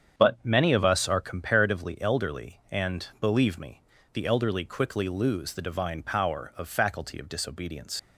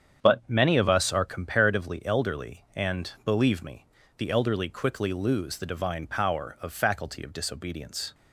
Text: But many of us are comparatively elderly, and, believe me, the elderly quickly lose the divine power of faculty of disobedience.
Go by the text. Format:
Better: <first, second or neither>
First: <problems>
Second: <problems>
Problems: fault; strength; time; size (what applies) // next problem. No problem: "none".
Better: second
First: starts louder than the rest; strong; until 1.2 s; 8 dB // leaves "disobedience" unfinished; at 7.9 s; 105 ms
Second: starts louder than the rest; strong; until 1.2 s; 8 dB